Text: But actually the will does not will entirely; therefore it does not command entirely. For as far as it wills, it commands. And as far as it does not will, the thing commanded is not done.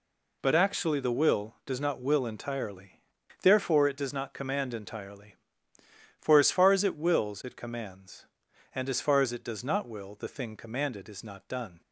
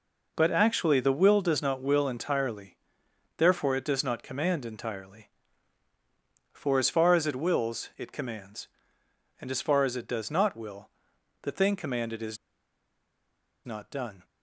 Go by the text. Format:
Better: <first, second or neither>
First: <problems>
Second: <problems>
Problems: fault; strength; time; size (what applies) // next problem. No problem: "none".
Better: first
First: none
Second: pauses between "is" and "not"; strong; at 12.3 s; 1.2 s long